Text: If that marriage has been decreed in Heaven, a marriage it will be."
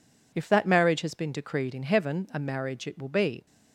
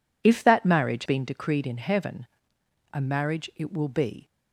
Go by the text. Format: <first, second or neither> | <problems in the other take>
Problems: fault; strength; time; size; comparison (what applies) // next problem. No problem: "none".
first | skips "has"; at 1.0 s